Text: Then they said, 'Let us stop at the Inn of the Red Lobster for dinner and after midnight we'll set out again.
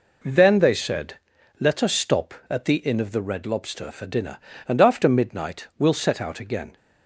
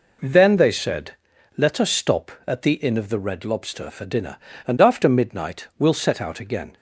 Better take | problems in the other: neither | none

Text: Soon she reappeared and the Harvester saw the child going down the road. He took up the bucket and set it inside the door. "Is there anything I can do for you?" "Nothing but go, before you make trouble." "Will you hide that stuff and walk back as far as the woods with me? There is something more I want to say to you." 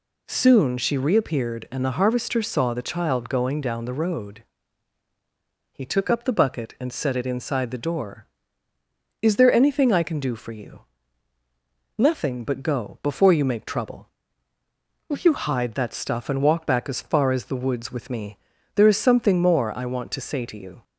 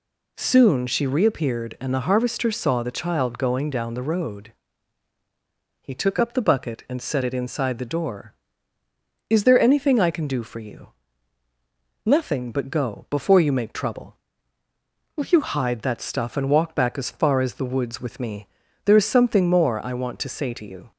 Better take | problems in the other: neither | none

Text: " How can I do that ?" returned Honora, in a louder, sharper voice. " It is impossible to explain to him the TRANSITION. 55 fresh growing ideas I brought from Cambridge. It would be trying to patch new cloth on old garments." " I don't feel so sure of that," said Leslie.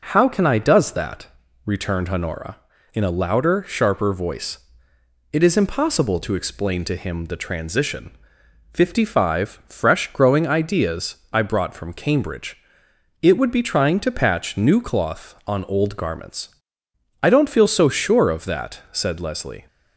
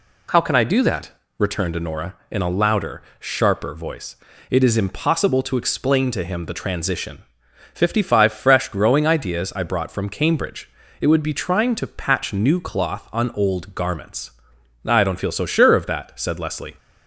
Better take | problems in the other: second | starts louder than the rest; until 1.0 s; 6.5 dB // says "does" for "do"; at 0.5 s // pauses between "ideas" and "I"; slight; at 11.1 s; 0.16 s long

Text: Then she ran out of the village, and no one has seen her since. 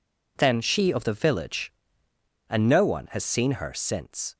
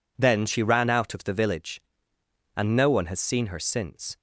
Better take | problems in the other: second | skips "ran out"; at 0.9 s

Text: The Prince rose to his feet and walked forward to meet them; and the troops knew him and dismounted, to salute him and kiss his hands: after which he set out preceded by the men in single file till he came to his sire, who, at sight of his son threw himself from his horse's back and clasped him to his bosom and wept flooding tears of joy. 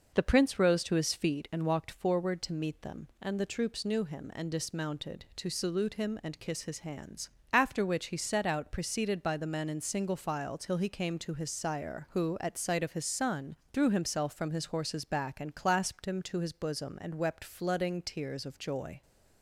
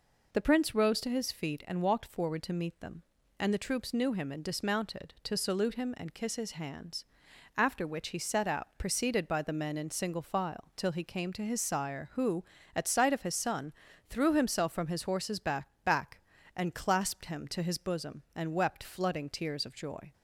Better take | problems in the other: first | pauses between "son" and "threw"; slight; at 13.7 s; 0.36 s long; slight in the first // says "back" twice; at 15.8 s

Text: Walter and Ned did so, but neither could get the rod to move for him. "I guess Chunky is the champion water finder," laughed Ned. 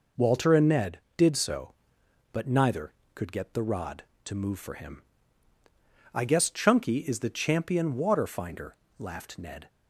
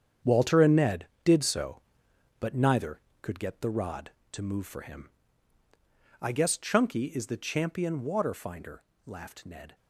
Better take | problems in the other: first | gets quieter; strong; throughout; 11 dB

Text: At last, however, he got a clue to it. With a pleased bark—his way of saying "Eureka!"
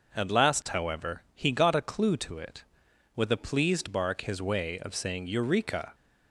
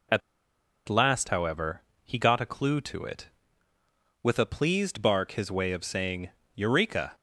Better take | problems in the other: first | pauses between "At" and "last"; noticeable; at 0.2 s; 0.68 s long // pauses between "saying" and "Eureka"; slight; at 6.3 s; 0.22 s long

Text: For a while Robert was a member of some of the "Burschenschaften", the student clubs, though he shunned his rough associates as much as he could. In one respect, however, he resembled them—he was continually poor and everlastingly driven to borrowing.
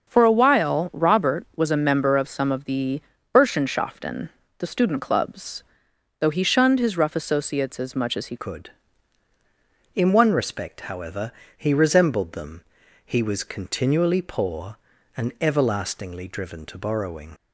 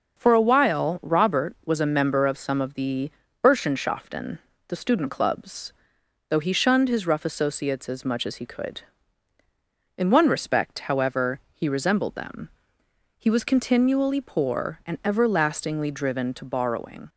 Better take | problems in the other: second | starts louder than the rest; until 1.1 s; 6.5 dB; also in the second // pauses between "the" and "Burschenschaften"; slight; at 3.0 s; 0.32 s long; slight in the second // changes voice at "could"; from 8.3 s on; 9.0 s long

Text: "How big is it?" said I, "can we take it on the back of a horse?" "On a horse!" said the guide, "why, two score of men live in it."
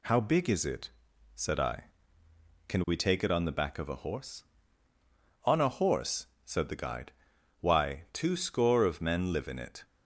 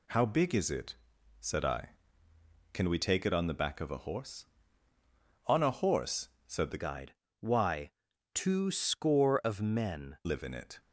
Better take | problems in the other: first | changes voice from "guide" to "men"; from 6.8 to 10.1 s; 3.3 s long

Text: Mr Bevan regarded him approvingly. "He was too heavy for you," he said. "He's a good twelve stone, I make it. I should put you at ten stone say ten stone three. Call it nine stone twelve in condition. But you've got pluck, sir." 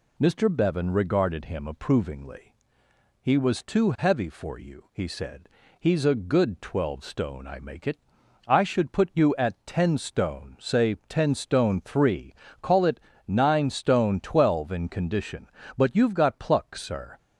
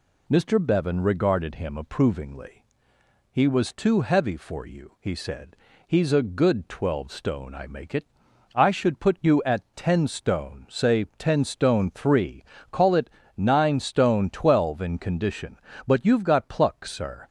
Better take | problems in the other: neither | pauses between "say" and "ten"; slight; the same in both // pauses between "it" and "nine"; slight; the same in both

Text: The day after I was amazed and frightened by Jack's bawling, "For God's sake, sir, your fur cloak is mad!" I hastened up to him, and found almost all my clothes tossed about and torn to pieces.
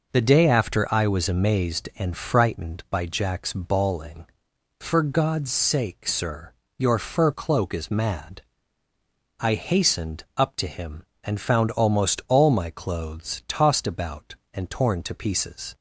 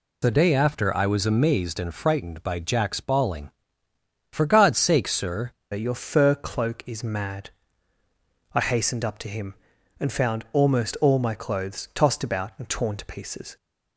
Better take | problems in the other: first | changes voice at "your"; from 5.7 s on; 7.8 s long

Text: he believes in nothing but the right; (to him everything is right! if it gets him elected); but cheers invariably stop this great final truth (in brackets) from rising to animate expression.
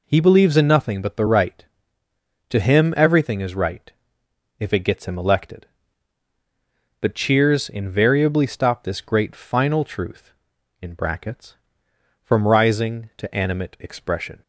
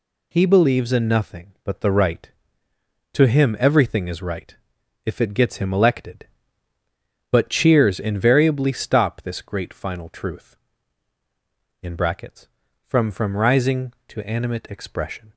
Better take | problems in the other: first | says "from" twice; at 13.1 s

